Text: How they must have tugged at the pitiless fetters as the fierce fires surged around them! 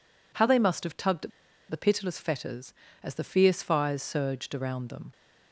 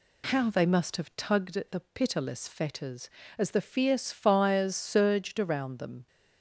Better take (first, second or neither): second